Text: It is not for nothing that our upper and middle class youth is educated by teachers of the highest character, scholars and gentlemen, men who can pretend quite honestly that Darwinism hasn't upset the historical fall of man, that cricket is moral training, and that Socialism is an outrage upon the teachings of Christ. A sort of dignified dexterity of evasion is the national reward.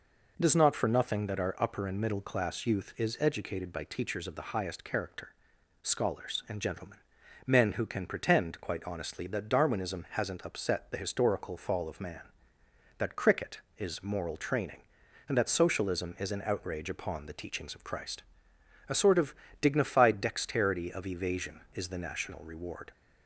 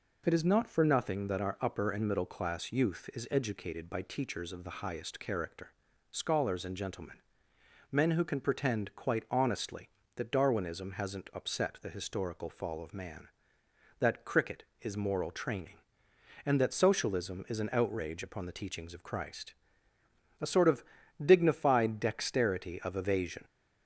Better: first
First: pauses between "of" and "dignified"; slight; at 19.3 s; 0.28 s long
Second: pauses between "of" and "dignified"; at 20.8 s; 0.40 s long // stops before "is the national reward"; at 23.4 s

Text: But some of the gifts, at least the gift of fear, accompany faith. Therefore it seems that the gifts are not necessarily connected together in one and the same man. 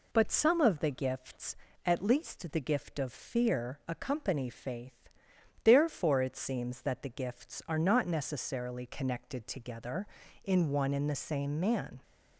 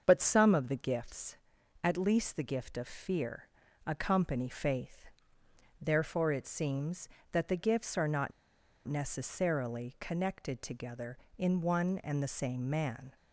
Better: first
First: none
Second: starts louder than the rest; until 1.0 s; 7 dB // pauses between "not" and "necessarily"; noticeable; at 8.3 s; 0.56 s long

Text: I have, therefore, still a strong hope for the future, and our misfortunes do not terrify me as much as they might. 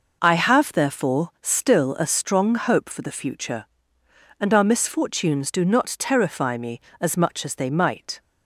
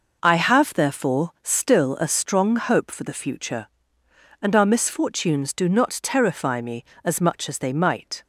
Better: neither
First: none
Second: none

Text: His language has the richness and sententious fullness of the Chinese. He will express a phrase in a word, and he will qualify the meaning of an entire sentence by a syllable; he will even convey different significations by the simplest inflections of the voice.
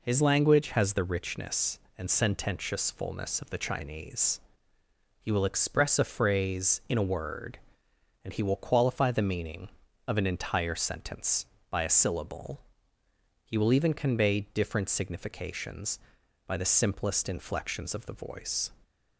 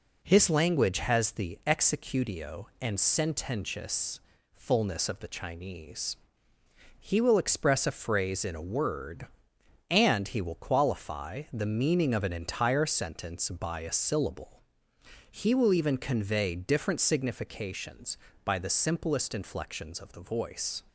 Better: first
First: none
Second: says "executio" for "richness"; at 1.6 s // pauses between "sententious" and "fullness"; slight; at 4.2 s; 0.32 s long

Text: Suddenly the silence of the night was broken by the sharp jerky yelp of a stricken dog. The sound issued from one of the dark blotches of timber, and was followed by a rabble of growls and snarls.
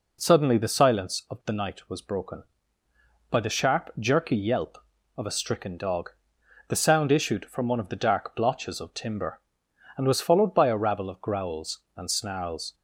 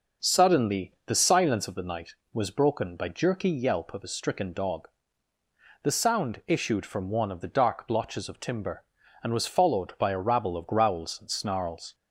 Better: first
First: none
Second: starts louder than the rest; noticeable; until 1.3 s; 6 dB // skips "the sharp"; at 3.0 s

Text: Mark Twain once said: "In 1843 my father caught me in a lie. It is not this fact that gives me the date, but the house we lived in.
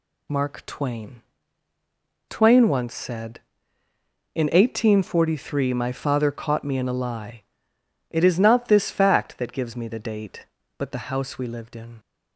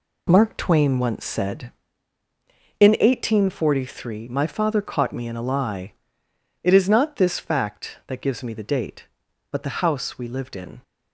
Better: second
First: says "Twain" twice; at 2.2 s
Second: none

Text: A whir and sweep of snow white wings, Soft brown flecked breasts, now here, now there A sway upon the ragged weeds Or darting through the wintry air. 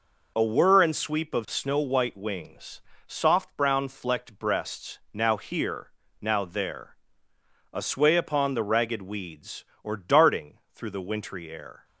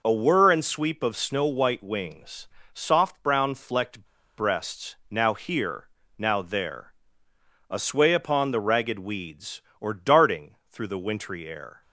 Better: first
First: pauses between "there" and "A"; noticeable; at 6.9 s; 0.78 s long // pauses between "darting" and "through"; slight; at 10.5 s; 0.16 s long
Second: pauses between "flecked" and "breasts"; slight; at 4.0 s; 0.33 s long // pauses between "there" and "A"; noticeable; at 6.9 s; 0.78 s long // pauses between "darting" and "through"; slight; at 10.5 s; 0.16 s long

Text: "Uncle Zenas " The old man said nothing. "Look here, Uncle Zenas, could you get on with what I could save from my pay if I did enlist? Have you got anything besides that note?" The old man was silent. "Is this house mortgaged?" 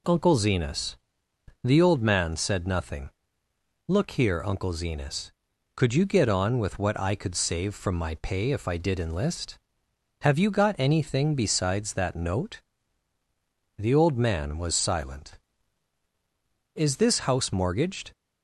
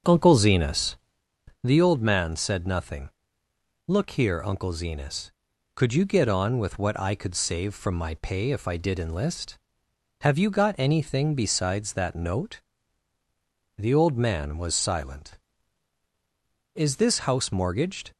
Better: first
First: none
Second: starts louder than the rest; until 1.2 s; 7 dB

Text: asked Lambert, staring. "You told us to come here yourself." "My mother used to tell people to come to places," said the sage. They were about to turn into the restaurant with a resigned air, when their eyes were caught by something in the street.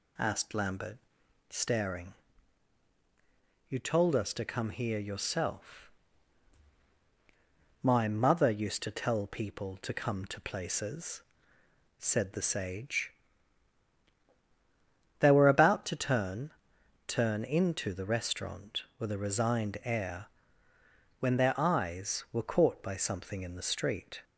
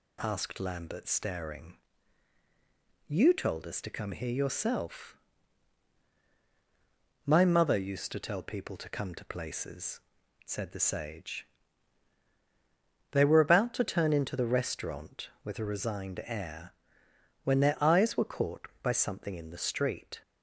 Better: second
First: says "turn" twice; at 17.0 s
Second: none

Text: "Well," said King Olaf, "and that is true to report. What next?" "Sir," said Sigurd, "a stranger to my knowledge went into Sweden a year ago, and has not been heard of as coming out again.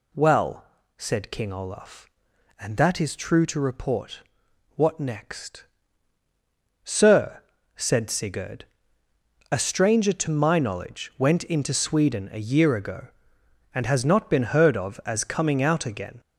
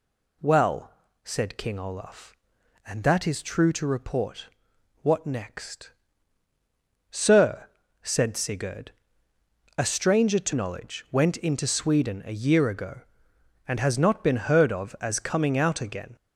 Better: first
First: none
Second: skips "my"; at 10.5 s

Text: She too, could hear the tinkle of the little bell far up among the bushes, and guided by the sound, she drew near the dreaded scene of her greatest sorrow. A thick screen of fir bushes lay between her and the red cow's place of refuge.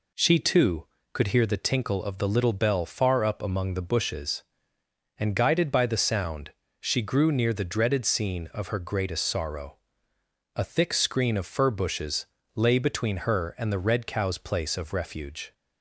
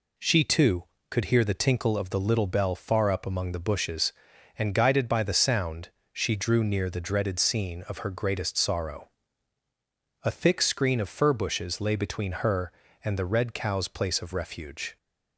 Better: second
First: says "grew" for "drew"; at 7.0 s // pauses between "bushes" and "lay"; slight; at 12.2 s; 0.30 s long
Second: none

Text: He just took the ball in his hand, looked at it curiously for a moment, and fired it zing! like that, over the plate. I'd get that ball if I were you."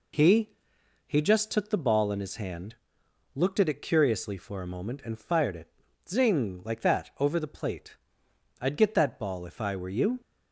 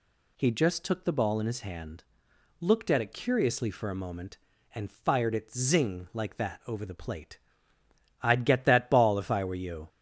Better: second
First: says "He" twice; at 1.0 s // pauses between "it" and "zing"; at 5.6 s; 0.40 s long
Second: none

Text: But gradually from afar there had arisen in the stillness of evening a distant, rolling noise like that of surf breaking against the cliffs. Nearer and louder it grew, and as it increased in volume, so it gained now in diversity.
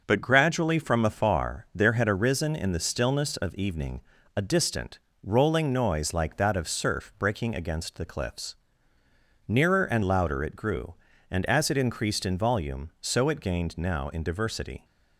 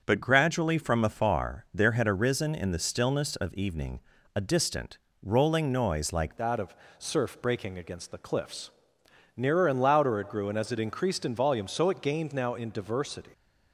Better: first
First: starts louder than the rest; until 1.0 s; 6.5 dB // pauses between "evening" and "a"; slight; at 4.0 s; 0.34 s long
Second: starts louder than the rest; until 1.0 s; 6.5 dB // pauses between "evening" and "a"; slight; at 4.0 s; 0.34 s long // changes voice at "that"; from 6.3 s on; 7.0 s long // pauses between "of" and "surf"; slight; at 6.7 s; 0.24 s long

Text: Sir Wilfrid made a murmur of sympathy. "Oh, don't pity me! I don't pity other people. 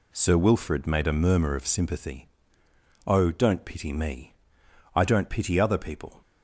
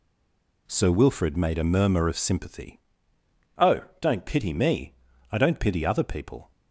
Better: first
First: none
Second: stays silent before the first word; slight; until 0.6 s; 0.6 s long

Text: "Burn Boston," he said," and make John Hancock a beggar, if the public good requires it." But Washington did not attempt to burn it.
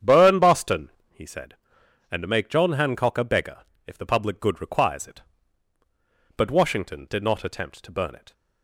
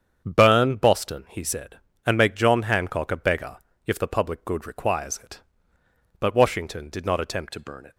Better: first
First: starts louder than the rest; strong; until 1.2 s; 8.5 dB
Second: starts louder than the rest; strong; until 1.2 s; 7.5 dB // changes voice at "to"; from 7.5 s on; 0.4 s long

